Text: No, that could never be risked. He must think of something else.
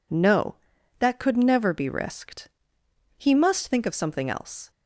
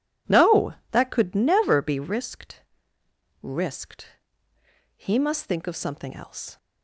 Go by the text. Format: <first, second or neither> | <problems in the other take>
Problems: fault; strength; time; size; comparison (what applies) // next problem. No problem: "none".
first | says "risked" twice; at 3.4 s